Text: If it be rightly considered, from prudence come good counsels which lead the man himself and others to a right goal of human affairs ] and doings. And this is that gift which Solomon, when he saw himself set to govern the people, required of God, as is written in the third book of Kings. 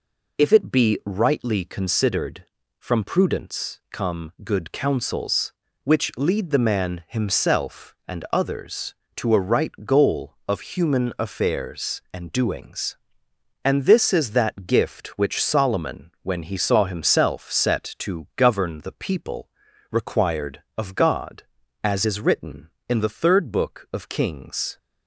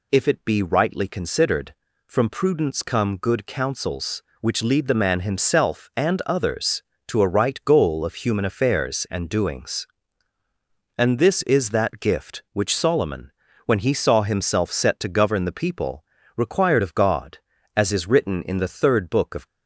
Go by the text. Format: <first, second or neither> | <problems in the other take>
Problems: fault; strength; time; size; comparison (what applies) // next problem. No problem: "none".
first | stops before "Kings"; at 19.4 s